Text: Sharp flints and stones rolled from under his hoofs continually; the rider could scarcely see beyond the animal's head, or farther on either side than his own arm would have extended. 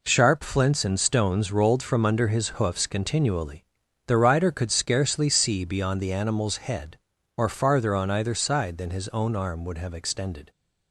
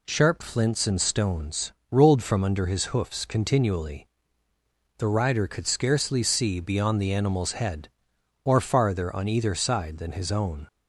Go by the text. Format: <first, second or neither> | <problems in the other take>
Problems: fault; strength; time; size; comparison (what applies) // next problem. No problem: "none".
first | pauses between "stones" and "rolled"; slight; at 1.7 s; 0.18 s long // stops before "arm would have extended"; at 10.6 s